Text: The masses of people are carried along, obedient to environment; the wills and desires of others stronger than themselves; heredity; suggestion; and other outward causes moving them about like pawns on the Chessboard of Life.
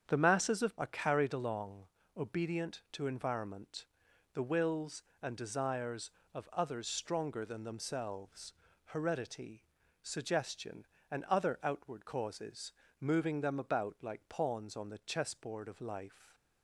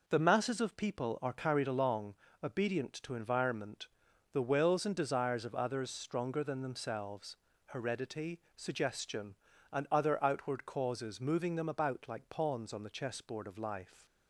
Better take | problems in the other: second | starts louder than the rest; strong; until 1.0 s; 8 dB // skips "people"; at 0.7 s // pauses between "causes" and "moving"; slight; at 12.7 s; 0.28 s long

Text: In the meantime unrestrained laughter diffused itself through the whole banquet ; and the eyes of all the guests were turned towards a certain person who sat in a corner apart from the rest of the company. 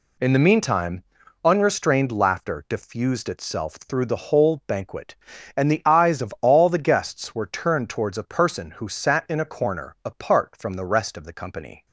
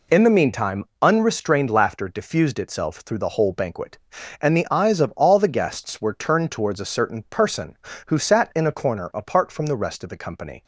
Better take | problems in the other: second | pauses between "meantime" and "unrestrained"; at 1.0 s; 0.40 s long; slight in the second // skips "certain"; at 8.2 s

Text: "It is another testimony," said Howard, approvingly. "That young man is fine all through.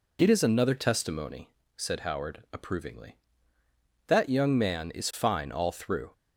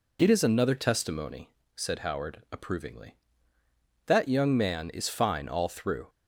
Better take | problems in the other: neither | none

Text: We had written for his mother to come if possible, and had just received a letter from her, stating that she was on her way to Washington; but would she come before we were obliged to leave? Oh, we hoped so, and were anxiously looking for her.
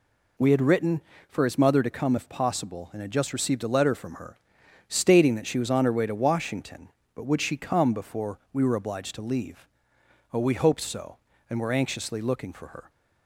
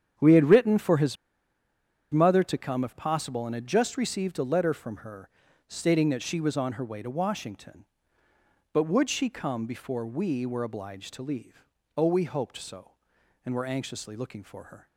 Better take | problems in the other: first | starts louder than the rest; strong; until 2.1 s; 8.5 dB // pauses between "his" and "mother"; noticeable; at 1.1 s; 0.96 s long

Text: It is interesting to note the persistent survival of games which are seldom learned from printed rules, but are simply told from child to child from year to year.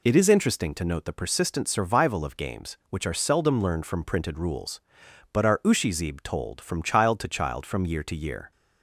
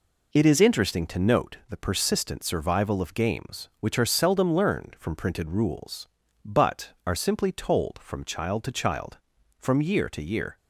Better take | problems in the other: second | says "ushizib" for "simply"; at 5.6 s

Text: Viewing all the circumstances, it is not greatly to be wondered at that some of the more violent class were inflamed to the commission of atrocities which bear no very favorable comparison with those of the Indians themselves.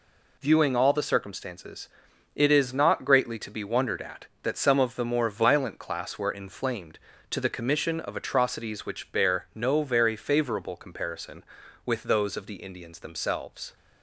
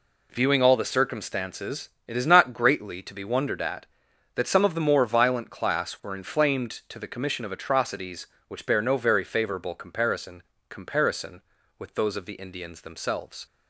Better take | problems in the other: first | says "comparison" twice; at 10.6 s

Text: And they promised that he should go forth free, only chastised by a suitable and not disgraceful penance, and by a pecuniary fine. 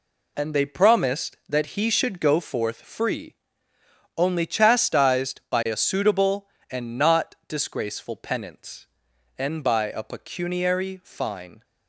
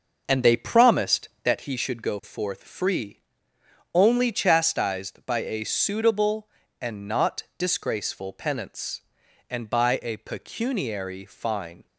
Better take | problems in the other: first | starts louder than the rest; noticeable; until 1.7 s; 6 dB

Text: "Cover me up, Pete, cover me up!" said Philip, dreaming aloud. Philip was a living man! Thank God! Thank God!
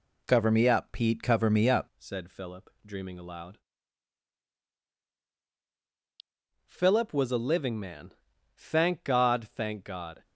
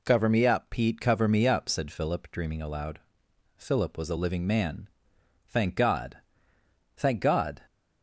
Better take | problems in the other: second | changes voice at "said"; from 1.9 s on; 8.3 s long

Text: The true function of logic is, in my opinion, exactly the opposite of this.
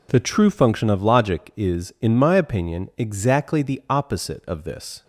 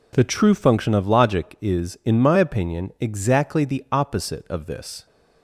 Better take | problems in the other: neither | none

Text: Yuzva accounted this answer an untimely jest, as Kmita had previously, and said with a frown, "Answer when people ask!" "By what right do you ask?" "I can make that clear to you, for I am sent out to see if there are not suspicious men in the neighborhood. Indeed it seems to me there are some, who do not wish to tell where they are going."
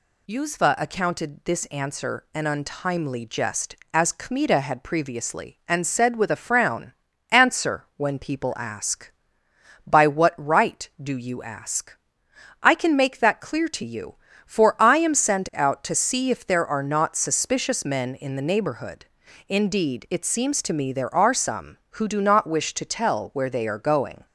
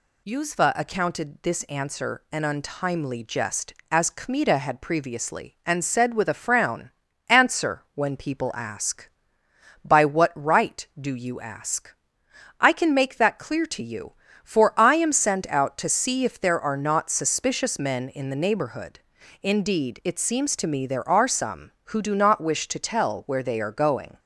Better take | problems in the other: neither | none

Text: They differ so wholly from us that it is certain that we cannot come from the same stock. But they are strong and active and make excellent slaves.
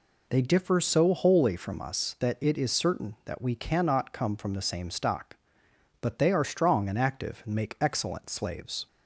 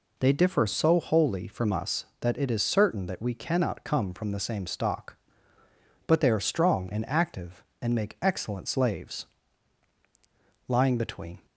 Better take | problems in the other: first | goes on to say "Lying between"; noticeable; from 10.6 s on; 0.78 s long

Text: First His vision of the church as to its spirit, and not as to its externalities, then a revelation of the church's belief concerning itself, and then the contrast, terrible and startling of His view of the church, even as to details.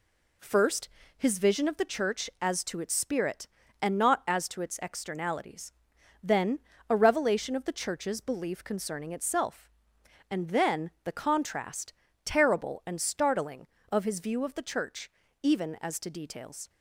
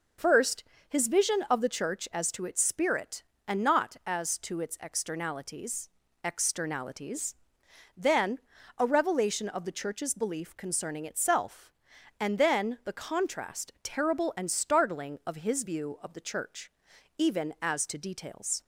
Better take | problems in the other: first | pauses between "First" and "His"; slight; at 0.6 s; 0.26 s long; slight in the first // says "externalities" twice; at 6.2 s // pauses between "then" and "a"; at 8.3 s; 0.38 s long; slight in the first

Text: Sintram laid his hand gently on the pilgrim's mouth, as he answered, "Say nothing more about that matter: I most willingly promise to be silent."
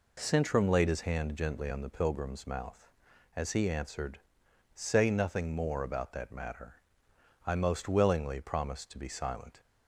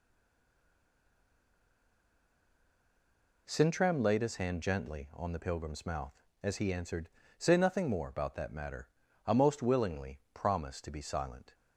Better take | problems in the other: first | stays silent before the first word; strong; until 3.4 s; 3.4 s long

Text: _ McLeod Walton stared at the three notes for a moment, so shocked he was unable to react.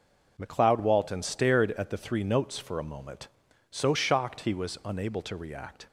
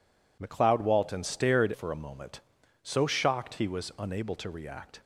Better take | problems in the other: first | skips "at the three notes"; at 1.7 s

